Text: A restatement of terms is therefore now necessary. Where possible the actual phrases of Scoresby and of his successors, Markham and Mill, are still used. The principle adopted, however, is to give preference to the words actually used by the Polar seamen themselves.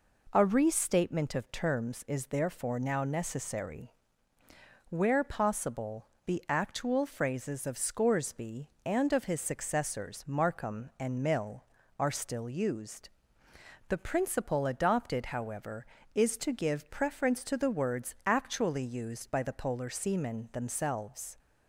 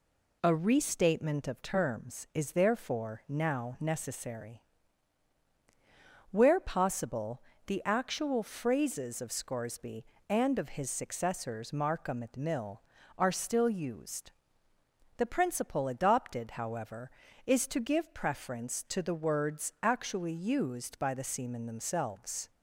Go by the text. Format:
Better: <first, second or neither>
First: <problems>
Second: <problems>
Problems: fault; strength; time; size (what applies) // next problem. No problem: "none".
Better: first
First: pauses between "possible" and "the"; slight; at 6.0 s; 0.18 s long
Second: pauses between "possible" and "the"; slight; at 7.4 s; 0.24 s long // skips "Polar"; at 21.2 s